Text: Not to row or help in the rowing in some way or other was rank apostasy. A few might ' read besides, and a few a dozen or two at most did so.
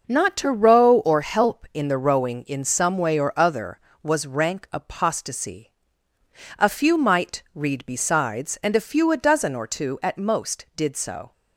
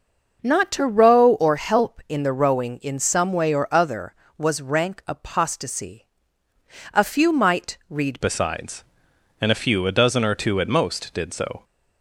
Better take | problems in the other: first | changes voice at "besides"; from 8.2 s on; 3.4 s long

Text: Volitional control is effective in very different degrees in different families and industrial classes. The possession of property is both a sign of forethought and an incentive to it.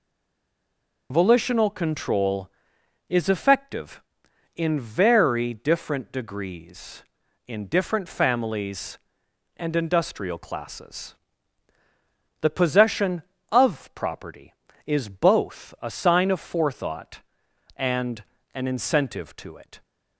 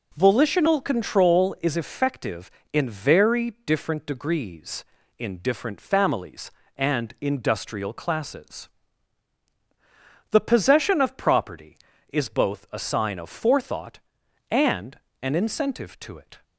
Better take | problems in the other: second | stays silent before the first word; until 1.1 s; 1.1 s long // pauses between "and" and "an"; slight; at 18.2 s; 0.30 s long; slight in the second

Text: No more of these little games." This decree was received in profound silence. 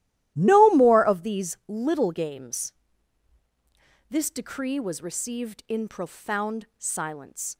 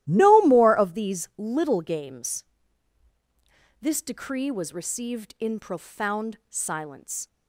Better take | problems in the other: neither | starts louder than the rest; strong; the same in both

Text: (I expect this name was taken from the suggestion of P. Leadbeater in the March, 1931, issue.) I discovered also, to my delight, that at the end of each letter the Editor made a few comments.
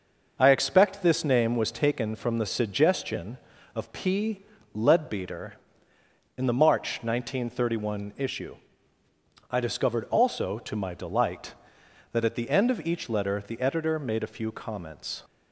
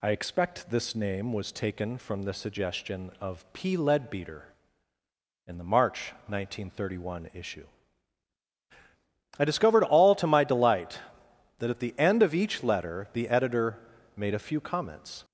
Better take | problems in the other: first | says "all" for "also"; at 9.8 s // pauses between "Editor" and "made"; at 13.7 s; 0.40 s long

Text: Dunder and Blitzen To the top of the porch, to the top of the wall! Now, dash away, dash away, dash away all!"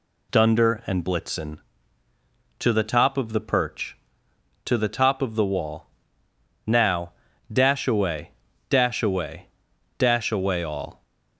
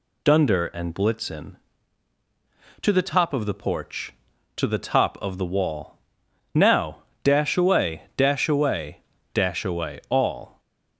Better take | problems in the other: second | says "perch" for "porch"; at 3.4 s

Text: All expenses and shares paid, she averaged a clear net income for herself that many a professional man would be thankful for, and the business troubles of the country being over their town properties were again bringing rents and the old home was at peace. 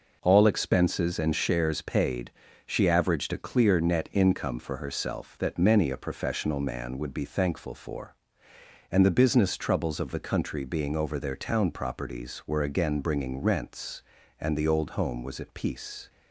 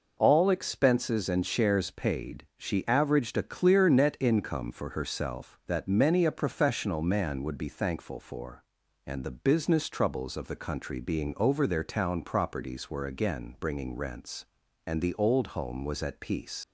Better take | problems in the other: first | leaves "peace" unfinished; at 16.6 s; 90 ms

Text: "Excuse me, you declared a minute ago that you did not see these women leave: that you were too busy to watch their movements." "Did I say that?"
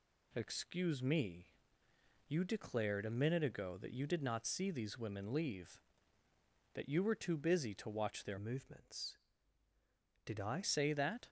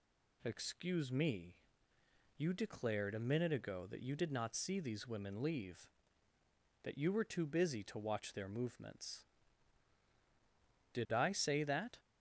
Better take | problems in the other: second | changes voice from "movements" to "I"; from 8.3 to 10.6 s; 2.3 s long

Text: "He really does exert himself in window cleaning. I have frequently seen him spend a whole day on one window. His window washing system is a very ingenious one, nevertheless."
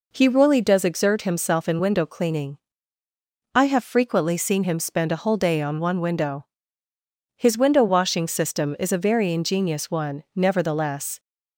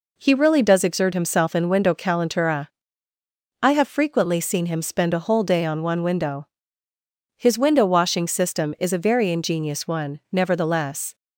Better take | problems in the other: first | says "calentura" for "cleaning"; at 1.9 s

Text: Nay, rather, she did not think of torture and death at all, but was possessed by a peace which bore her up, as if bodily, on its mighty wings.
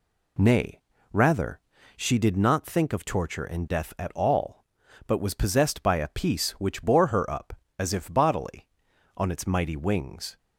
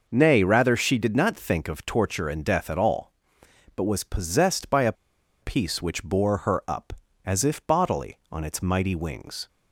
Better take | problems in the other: first | pauses between "a" and "peace"; noticeable; at 4.9 s; 0.48 s long

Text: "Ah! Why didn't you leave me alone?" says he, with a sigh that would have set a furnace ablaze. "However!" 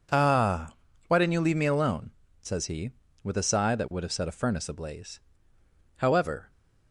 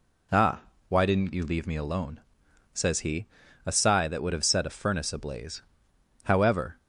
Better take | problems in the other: first | skips "with"; at 3.4 s

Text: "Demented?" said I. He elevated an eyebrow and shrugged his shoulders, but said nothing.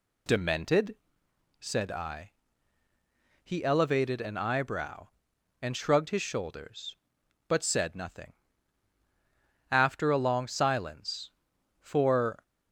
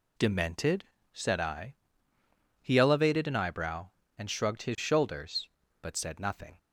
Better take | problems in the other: second | goes on to say "After a long silence for"; strong; from 9.7 s on; 2.7 s long

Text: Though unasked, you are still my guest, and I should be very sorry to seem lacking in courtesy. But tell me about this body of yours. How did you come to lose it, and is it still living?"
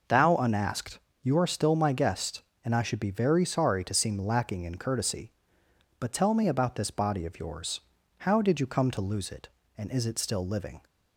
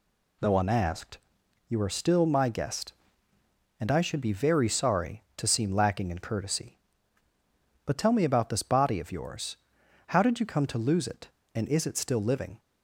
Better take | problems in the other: second | says "Thou" for "Though"; at 0.0 s

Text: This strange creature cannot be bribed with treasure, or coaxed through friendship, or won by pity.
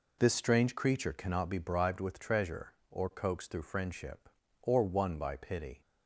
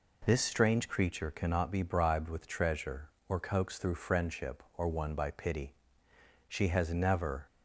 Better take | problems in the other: first | goes on to say "She has never"; noticeable; from 6.4 s on; 0.98 s long

